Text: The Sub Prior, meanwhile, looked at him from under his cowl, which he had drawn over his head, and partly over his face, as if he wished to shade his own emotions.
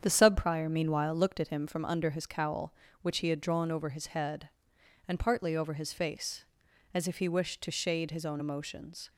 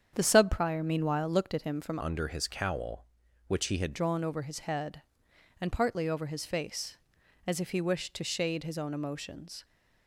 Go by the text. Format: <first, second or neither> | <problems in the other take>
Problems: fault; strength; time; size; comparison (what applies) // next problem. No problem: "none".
first | starts louder than the rest; strong; until 1.1 s; 8 dB; strong in the first // changes voice from "under" to "had"; from 2.0 to 3.9 s; 1.9 s long